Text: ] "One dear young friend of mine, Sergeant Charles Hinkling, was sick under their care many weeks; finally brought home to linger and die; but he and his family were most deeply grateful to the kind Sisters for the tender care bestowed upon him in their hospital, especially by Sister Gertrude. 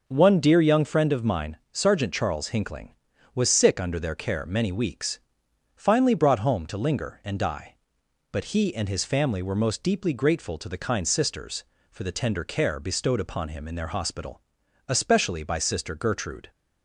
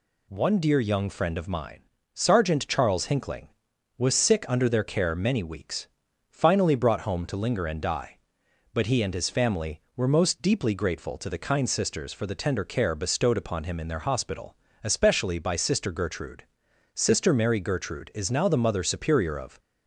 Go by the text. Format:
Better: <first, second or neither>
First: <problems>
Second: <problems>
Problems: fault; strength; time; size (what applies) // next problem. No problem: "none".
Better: first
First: none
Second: goes on to say "Sister Mary Gertrude is now the Mother Superior of"; strong; from 16.9 s on; 2.6 s long